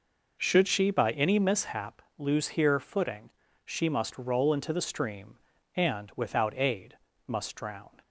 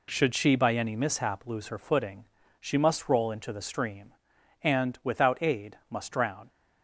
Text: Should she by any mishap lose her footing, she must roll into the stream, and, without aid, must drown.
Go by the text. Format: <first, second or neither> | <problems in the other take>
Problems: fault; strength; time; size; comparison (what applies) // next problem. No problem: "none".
second | pauses between "mishap" and "lose"; slight; at 1.9 s; 0.20 s long // says "here" for "her"; at 2.4 s